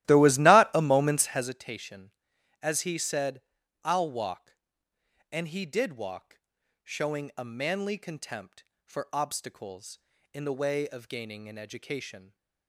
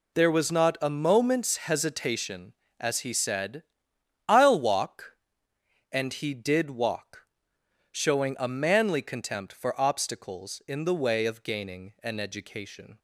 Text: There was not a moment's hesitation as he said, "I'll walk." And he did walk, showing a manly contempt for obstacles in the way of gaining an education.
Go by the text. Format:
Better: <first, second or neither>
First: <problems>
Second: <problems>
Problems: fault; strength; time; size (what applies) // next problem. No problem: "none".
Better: second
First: starts louder than the rest; strong; until 1.6 s; 15 dB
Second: none